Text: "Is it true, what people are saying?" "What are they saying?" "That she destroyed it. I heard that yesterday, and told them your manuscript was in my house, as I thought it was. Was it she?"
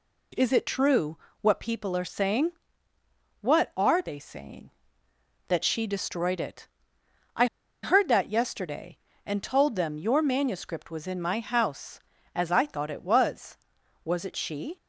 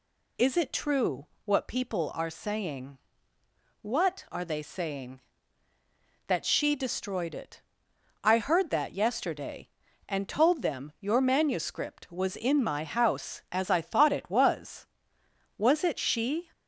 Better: second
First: pauses between "I" and "heard"; at 7.4 s; 0.38 s long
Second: none

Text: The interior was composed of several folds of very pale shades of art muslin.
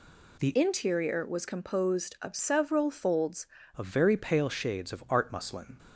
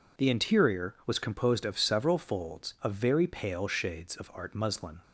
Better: second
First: changes voice from "interior" to "folds"; from 0.5 to 3.4 s; 2.9 s long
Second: none

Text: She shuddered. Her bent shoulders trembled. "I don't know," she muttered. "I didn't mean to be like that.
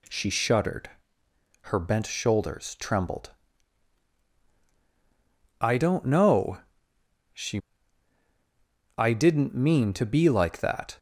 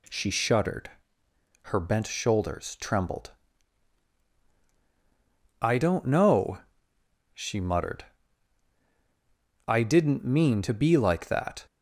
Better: second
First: skips "muttered"; at 8.2 s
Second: none

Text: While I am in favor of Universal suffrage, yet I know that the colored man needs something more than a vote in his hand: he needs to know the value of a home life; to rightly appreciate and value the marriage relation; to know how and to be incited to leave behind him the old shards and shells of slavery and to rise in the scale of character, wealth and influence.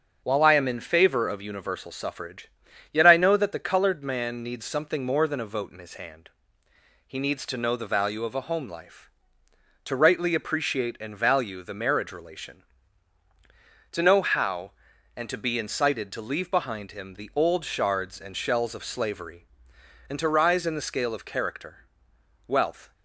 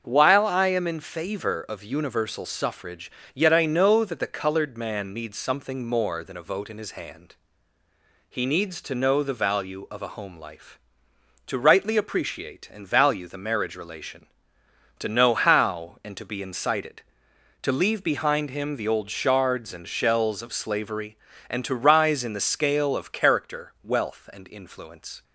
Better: second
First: starts louder than the rest; until 1.2 s; 6.5 dB // stops before "and influence"; at 22.9 s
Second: starts louder than the rest; until 1.0 s; 6.5 dB

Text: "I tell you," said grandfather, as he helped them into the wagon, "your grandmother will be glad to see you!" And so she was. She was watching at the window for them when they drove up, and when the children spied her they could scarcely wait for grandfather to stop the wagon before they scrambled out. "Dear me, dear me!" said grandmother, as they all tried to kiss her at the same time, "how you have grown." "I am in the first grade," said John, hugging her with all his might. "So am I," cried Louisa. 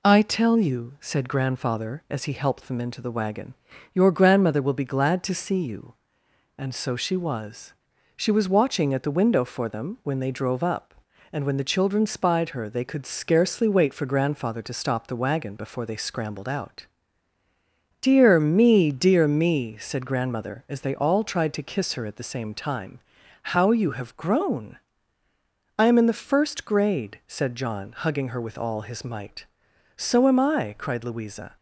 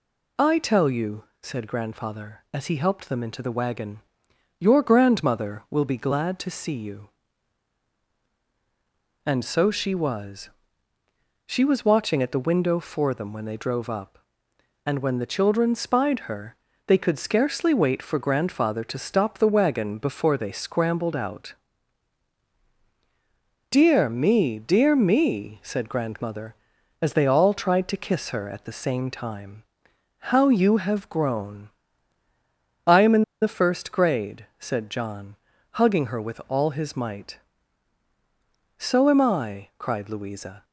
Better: first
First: none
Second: pauses between "her" and "they"; slight; at 16.5 s; 0.32 s long // pauses between "in" and "the"; slight; at 33.2 s; 0.19 s long

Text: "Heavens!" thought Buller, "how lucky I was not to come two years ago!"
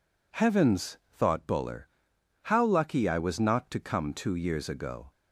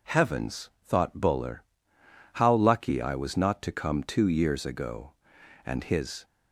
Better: first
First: none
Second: goes on to say "And his"; from 5.6 s on; 0.60 s long

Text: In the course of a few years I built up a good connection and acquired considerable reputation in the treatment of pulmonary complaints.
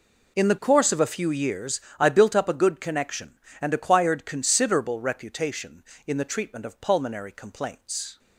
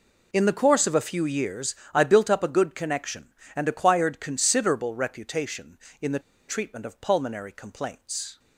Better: first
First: pauses between "years" and "I"; slight; at 1.7 s; 0.20 s long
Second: pauses between "years" and "I"; slight; at 1.7 s; 0.20 s long // pauses between "the" and "treatment"; slight; at 6.1 s; 0.28 s long

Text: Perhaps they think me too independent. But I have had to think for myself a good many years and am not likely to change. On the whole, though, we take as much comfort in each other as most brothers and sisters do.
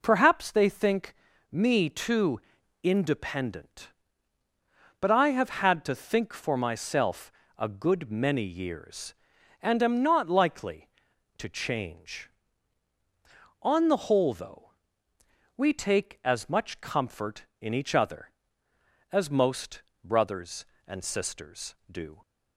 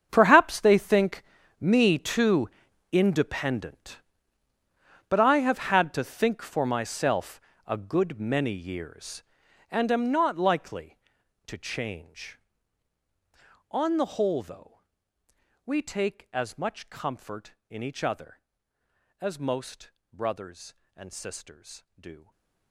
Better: first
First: pauses between "think" and "me"; at 1.1 s; 0.38 s long // pauses between "too" and "independent"; at 2.3 s; 0.42 s long // pauses between "myself" and "a"; slight; at 7.3 s; 0.26 s long // pauses between "most" and "brothers"; slight; at 19.8 s; 0.22 s long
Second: gets quieter; strong; throughout; 17 dB // pauses between "think" and "me"; at 1.2 s; 0.38 s long // pauses between "too" and "independent"; at 2.4 s; 0.42 s long // pauses between "myself" and "a"; slight; at 7.4 s; 0.26 s long // pauses between "most" and "brothers"; slight; at 19.9 s; 0.22 s long // stays silent after the last word; slight; from 22.1 s on; 0.6 s long

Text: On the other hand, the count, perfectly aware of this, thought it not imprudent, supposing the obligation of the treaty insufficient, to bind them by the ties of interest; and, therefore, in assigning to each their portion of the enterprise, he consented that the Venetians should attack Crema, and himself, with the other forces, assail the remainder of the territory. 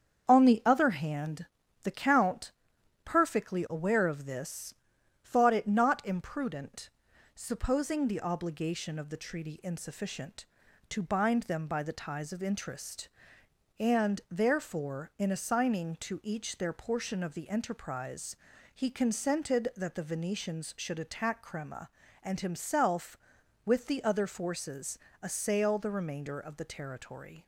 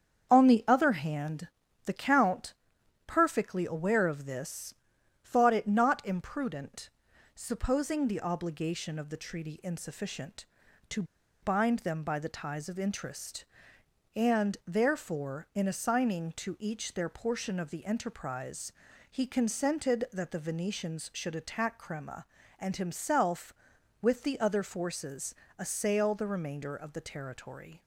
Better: first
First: starts louder than the rest; strong; until 1.3 s; 7.5 dB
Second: starts louder than the rest; strong; until 1.3 s; 7.5 dB // pauses between "to" and "bind"; at 11.0 s; 0.39 s long

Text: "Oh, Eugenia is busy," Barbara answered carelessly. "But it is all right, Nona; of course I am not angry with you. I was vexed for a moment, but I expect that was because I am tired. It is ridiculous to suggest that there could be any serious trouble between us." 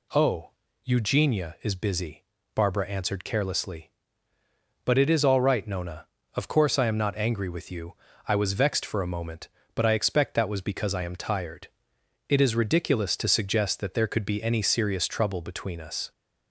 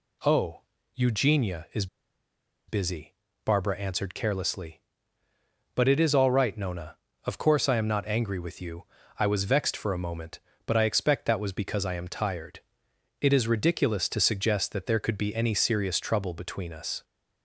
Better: first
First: none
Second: pauses between "is" and "busy"; noticeable; at 1.8 s; 0.82 s long

